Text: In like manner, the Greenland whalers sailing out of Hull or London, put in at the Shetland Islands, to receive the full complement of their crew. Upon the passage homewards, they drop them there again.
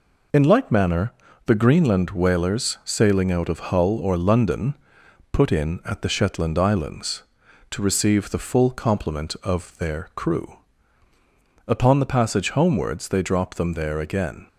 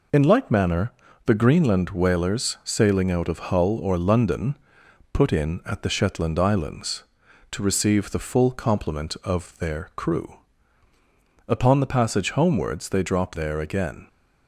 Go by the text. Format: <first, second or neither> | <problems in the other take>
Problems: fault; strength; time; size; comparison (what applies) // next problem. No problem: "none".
first | skips "them"; at 13.3 s